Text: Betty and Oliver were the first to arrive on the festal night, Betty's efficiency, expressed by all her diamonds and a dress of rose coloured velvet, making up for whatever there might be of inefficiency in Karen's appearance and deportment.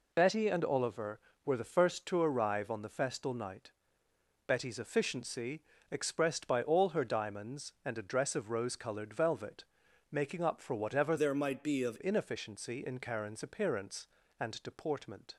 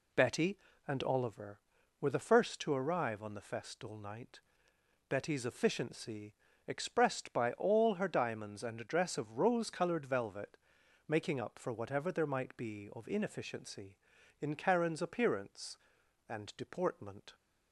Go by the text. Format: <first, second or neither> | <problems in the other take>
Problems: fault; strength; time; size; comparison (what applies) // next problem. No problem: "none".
second | changes voice from "there" to "of"; from 11.1 to 11.9 s; 0.8 s long